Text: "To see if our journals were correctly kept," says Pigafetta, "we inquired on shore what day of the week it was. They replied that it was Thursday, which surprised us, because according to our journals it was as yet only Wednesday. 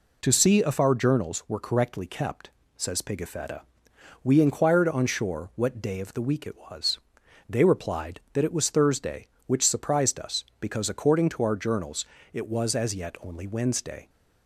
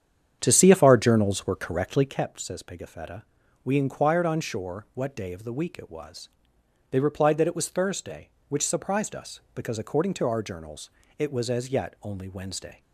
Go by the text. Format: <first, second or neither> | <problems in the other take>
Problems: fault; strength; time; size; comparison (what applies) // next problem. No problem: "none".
first | starts louder than the rest; strong; until 2.2 s; 8.5 dB // pauses between "journals" and "it"; slight; at 10.8 s; 0.28 s long; slight in the first